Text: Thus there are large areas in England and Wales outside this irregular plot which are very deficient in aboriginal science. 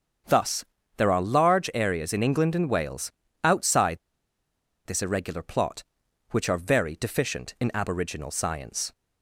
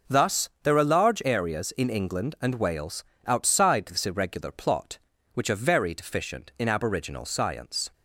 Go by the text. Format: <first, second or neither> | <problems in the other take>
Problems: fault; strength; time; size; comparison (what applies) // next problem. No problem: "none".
second | starts louder than the rest; strong; until 1.5 s; 7.5 dB // pauses between "Thus" and "there"; slight; at 0.6 s; 0.32 s long // pauses between "Wales" and "outside"; slight; at 3.1 s; 0.32 s long; slight in the second // pauses between "outside" and "this"; noticeable; at 3.9 s; 0.86 s long